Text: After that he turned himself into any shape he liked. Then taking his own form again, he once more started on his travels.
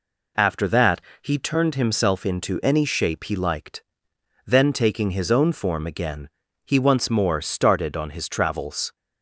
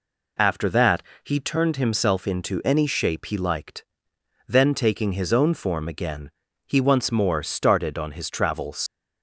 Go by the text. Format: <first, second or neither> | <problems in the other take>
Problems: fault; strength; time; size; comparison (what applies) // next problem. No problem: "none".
first | pauses between "that" and "he"; slight; at 1.0 s; 0.20 s long; slight in the first // leaves "travels" unfinished; at 8.8 s; 100 ms